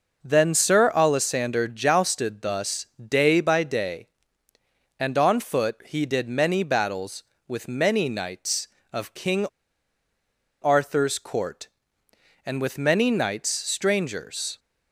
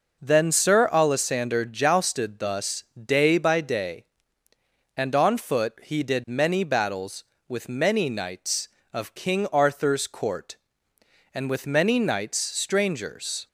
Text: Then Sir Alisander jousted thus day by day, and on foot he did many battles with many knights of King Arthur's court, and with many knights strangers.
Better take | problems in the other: second | pauses between "thus" and "day"; slight; at 2.8 s; 0.16 s long; slight in the second // pauses between "King" and "Arthur's"; at 9.4 s; 1.1 s long

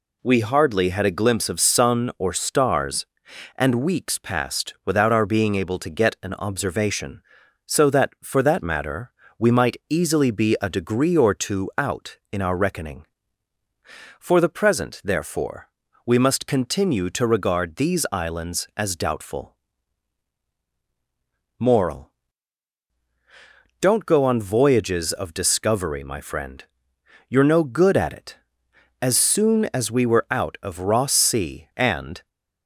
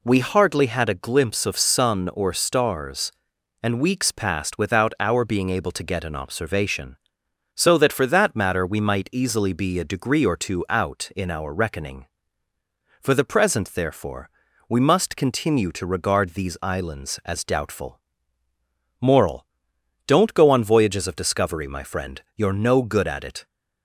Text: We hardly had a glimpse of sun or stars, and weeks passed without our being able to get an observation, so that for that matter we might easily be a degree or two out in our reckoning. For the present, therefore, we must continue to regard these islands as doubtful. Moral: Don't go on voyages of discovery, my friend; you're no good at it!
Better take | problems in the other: second | pauses between "matter" and "we"; slight; at 9.1 s; 0.26 s long // goes on to say "As soon as we were out of Ross Sea and"; strong; from 28.9 s on; 3.2 s long

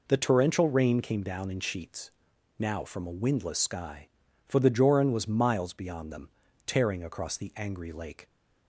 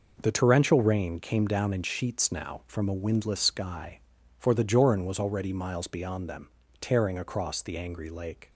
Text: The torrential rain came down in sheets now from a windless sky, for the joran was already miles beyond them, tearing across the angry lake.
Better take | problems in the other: second | pauses between "sheets" and "now"; noticeable; at 2.1 s; 0.48 s long // skips "already"; at 5.2 s

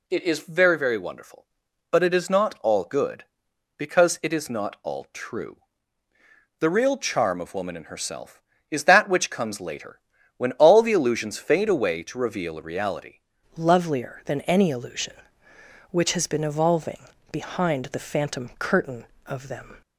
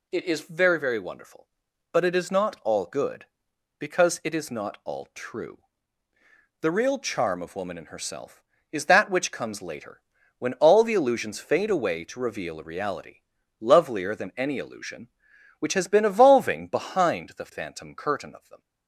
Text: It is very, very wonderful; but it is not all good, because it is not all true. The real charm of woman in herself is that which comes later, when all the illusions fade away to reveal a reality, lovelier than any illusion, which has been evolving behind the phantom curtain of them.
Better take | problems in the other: second | changes voice at "lovelier"; from 13.5 s on; 6.3 s long // pauses between "evolving" and "behind"; slight; at 16.9 s; 0.32 s long

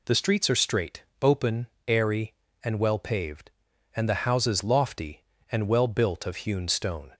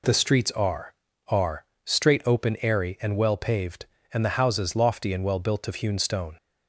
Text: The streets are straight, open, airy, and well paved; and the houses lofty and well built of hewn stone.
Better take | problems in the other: first | says "are" twice; at 1.2 s

